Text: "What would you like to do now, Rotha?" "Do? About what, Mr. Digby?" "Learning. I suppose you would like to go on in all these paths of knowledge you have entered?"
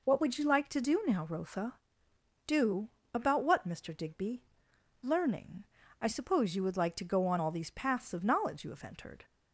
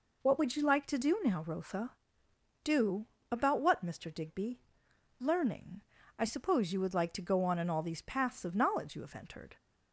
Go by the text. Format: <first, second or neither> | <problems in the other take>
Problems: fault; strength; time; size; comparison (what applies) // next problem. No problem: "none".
second | skips "in"; at 7.3 s